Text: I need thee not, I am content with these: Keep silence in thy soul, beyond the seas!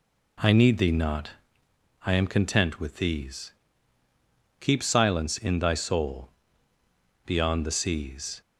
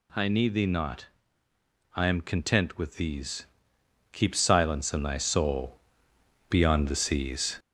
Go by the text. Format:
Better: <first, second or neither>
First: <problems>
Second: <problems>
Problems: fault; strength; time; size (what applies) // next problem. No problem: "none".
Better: first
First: none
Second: gets louder; slight; throughout; 3 dB